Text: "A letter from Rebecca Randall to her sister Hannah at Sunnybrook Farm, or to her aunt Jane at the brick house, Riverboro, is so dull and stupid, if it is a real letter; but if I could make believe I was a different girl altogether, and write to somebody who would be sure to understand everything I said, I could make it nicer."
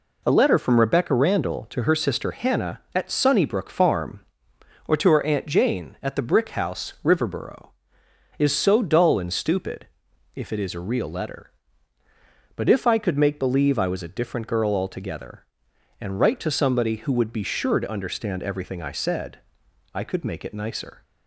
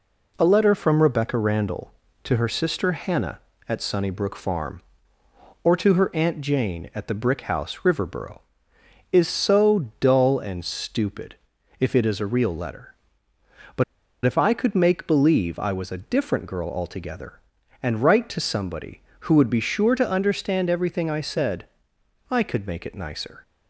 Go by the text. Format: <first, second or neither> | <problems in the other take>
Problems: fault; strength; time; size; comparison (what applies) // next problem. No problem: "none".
first | pauses between "but" and "if"; at 13.8 s; 0.42 s long